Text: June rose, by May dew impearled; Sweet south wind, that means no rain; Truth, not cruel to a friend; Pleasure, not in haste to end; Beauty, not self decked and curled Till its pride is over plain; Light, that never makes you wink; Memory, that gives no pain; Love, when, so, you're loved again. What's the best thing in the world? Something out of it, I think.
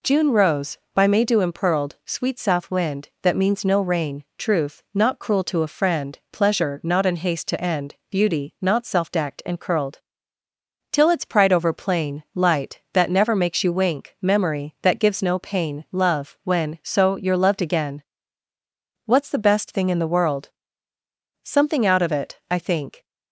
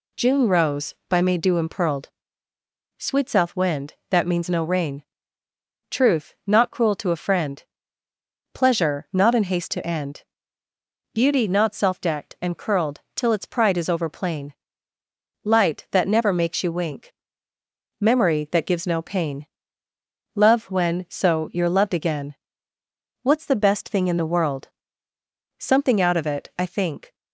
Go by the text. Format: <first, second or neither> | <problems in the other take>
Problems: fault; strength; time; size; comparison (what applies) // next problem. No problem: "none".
second | pauses between "curled" and "Till"; noticeable; at 9.9 s; 0.92 s long // skips "is"; at 11.5 s